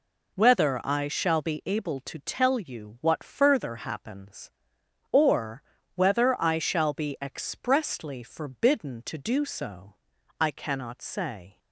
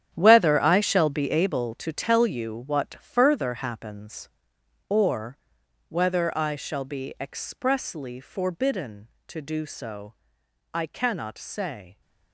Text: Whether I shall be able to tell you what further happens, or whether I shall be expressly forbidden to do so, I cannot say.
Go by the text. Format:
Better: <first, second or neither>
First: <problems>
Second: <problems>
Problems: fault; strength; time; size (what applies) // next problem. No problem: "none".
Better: first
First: pauses between "or" and "whether"; slight; at 5.6 s; 0.32 s long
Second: gets quieter; strong; throughout; 13 dB // pauses between "or" and "whether"; noticeable; at 5.3 s; 0.52 s long